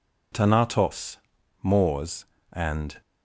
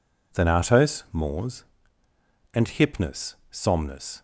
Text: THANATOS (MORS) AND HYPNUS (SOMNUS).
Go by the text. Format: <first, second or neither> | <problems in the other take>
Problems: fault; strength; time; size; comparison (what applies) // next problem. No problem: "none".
second | stops before "HYPNUS SOMNUS"; at 3.0 s